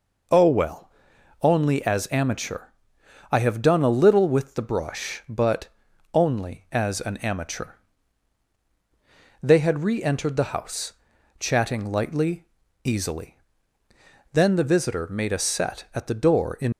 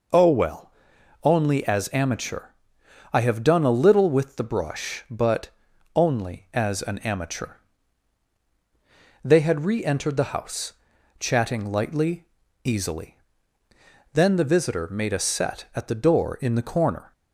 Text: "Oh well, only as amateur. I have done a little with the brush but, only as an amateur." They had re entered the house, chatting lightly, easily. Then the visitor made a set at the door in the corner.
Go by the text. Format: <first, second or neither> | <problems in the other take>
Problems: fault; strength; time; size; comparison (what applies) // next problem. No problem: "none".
second | stops before "the corner"; at 16.7 s